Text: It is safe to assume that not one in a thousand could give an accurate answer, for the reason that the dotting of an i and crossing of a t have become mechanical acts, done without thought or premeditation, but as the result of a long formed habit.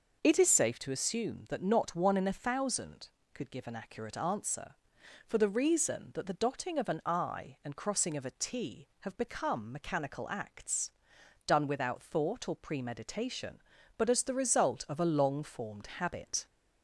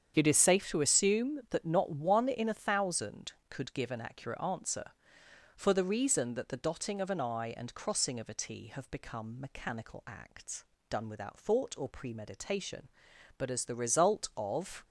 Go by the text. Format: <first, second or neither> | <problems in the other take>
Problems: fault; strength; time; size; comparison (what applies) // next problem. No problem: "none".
first | starts louder than the rest; strong; until 1.1 s; 8 dB // stops before "a long formed habit"; at 14.8 s